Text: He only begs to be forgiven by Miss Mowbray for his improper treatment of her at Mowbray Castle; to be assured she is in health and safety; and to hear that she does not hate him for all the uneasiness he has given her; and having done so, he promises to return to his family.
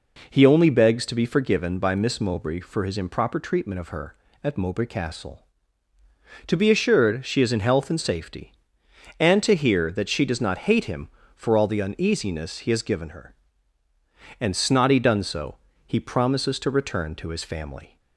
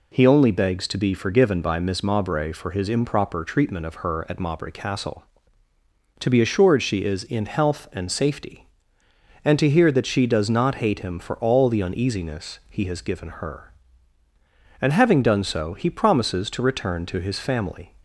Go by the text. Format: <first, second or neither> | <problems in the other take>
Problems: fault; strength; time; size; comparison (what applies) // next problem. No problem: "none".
second | says "snotty" for "having"; at 14.5 s